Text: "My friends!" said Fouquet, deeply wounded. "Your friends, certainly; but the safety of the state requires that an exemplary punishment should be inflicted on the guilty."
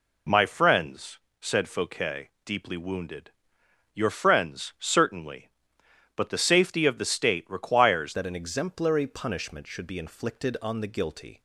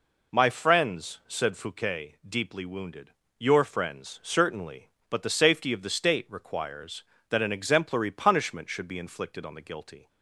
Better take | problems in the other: second | changes voice at "that"; from 8.1 s on; 3.3 s long

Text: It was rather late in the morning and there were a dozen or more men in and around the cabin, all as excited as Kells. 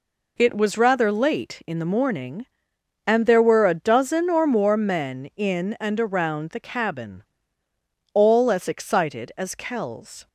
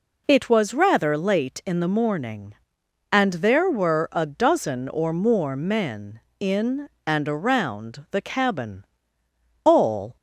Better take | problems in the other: first | stops before "as excited as Kells"; at 10.1 s

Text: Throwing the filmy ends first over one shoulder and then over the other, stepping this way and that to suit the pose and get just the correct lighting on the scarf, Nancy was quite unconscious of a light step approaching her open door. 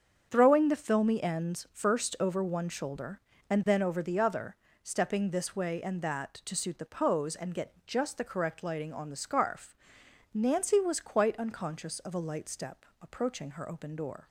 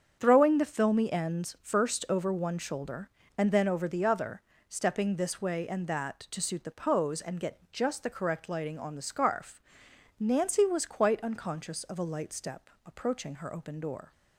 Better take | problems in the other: neither | starts louder than the rest; strong; the same in both // pauses between "step" and "approaching"; slight; the same in both

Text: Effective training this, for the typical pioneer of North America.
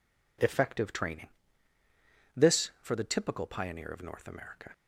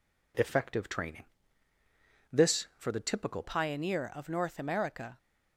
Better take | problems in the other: first | pauses between "training" and "this"; at 1.2 s; 1.0 s long; also in the first // changes voice at "pioneer"; from 3.4 s on; 1.7 s long

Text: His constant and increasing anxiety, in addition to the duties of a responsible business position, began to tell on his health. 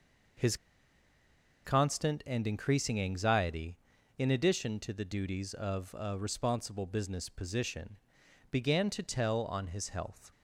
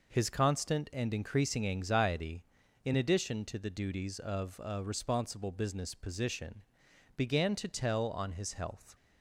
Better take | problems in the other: second | pauses between "His" and "constant"; at 0.5 s; 1.0 s long

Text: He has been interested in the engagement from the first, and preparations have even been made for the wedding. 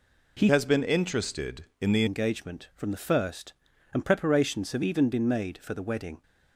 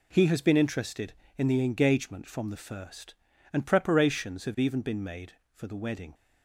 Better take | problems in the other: second | changes voice from "has" to "the"; from 0.4 to 2.0 s; 1.6 s long

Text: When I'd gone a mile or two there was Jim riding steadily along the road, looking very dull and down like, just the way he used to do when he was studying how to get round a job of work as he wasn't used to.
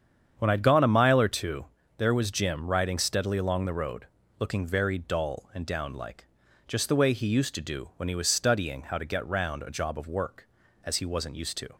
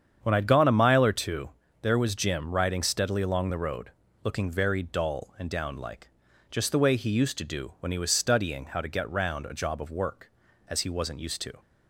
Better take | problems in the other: neither | starts louder than the rest; strong; the same in both // pauses between "two" and "there"; slight; the same in both

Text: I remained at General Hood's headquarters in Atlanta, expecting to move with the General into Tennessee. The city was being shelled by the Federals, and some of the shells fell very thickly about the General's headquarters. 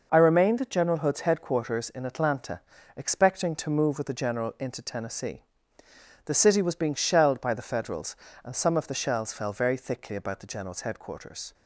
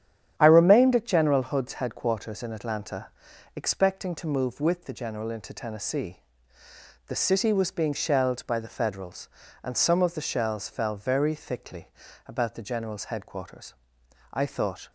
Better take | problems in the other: first | starts louder than the rest; strong; until 1.3 s; 9.5 dB // pauses between "thickly" and "about"; at 11.8 s; 0.38 s long // goes on to say "I thought"; from 14.3 s on; 0.60 s long

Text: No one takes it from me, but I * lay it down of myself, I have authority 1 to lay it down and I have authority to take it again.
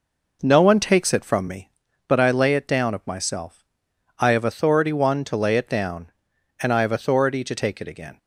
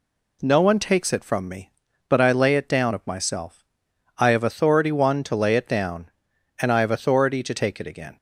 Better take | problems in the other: second | starts louder than the rest; noticeable; until 1.6 s; 5 dB

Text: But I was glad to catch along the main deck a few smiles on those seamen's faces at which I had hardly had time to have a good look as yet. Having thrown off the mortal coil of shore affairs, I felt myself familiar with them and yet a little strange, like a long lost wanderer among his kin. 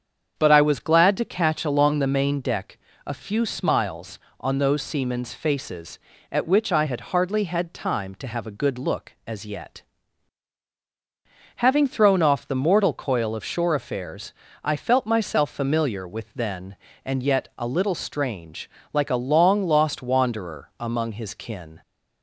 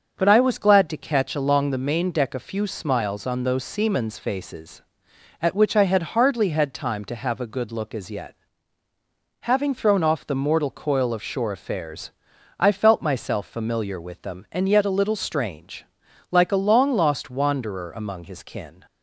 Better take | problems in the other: second | starts louder than the rest; strong; until 1.3 s; 7.5 dB; also in the second // pauses between "deck" and "a"; slight; at 2.7 s; 0.28 s long // says "then" for "them"; at 16.3 s

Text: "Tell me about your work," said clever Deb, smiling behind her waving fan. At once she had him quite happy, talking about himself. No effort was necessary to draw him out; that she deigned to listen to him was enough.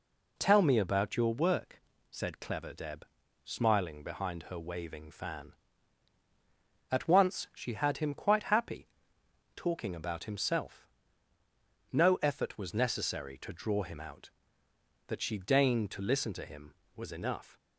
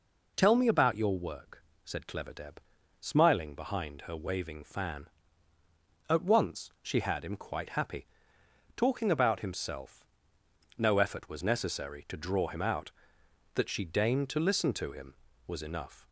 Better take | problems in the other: neither | none

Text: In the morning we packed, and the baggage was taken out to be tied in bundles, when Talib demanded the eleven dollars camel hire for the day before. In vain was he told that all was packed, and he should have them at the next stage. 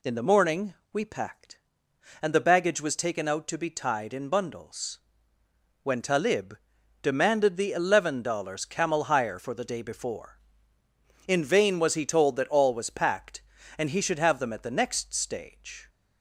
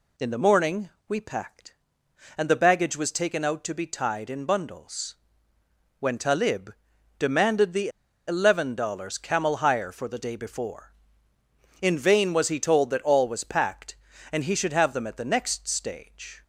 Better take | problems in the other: first | pauses between "morning" and "we"; slight; at 0.8 s; 0.20 s long; slight in the first // pauses between "Talib" and "demanded"; noticeable; at 6.7 s; 0.46 s long; noticeable in the first // pauses between "the" and "eleven"; at 7.8 s; 0.39 s long

